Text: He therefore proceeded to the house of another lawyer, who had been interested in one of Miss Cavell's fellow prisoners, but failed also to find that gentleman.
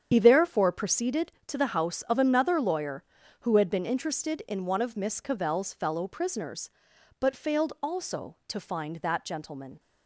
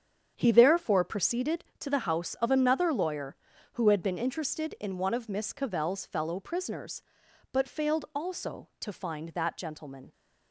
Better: second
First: loses the start of "He"; at 0.1 s; 80 ms // starts louder than the rest; strong; until 1.1 s; 8 dB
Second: starts louder than the rest; strong; until 1.3 s; 8 dB

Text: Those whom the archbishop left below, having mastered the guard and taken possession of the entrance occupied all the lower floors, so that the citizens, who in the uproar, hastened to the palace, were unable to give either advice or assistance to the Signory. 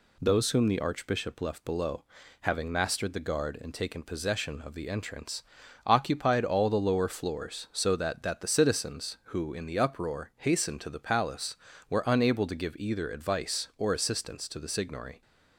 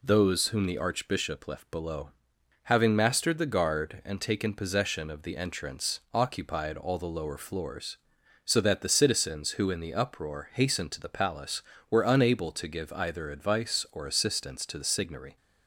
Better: second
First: pauses between "entrance" and "occupied"; at 5.4 s; 0.42 s long // says "that" twice; at 8.2 s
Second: none

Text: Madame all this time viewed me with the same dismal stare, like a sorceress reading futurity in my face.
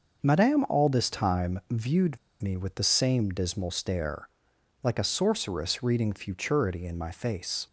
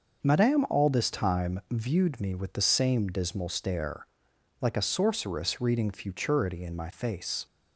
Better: second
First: pauses between "viewed" and "me"; slight; at 2.1 s; 0.22 s long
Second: none

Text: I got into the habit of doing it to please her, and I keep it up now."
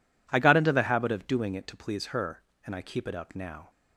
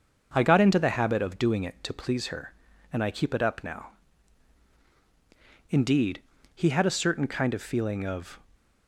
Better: first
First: none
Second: starts louder than the rest; until 1.3 s; 6.5 dB // goes on to say "Indeed he had a certain kind of feeling of"; strong; from 5.6 s on; 2.7 s long

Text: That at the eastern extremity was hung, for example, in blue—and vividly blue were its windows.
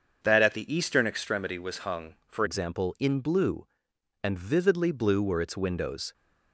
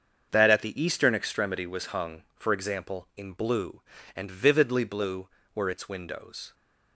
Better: second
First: starts louder than the rest; until 1.2 s; 7 dB // changes voice at "example"; from 2.4 s on; 3.7 s long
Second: starts louder than the rest; until 1.3 s; 7 dB

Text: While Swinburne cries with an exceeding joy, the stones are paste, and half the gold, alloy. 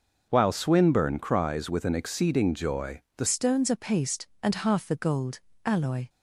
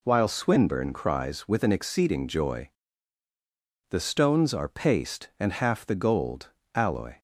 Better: second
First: changes voice at "stones"; from 3.2 s on; 2.8 s long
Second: none

